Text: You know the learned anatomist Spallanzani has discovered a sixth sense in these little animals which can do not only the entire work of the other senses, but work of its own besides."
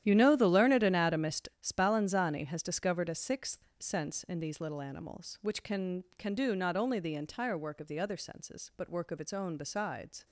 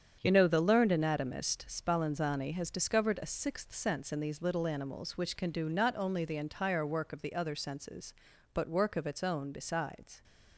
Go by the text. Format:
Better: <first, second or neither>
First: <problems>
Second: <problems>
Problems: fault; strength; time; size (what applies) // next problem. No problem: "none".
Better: second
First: starts louder than the rest; strong; until 1.0 s; 11.5 dB // says "can" twice; at 6.1 s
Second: starts louder than the rest; strong; until 1.2 s; 8 dB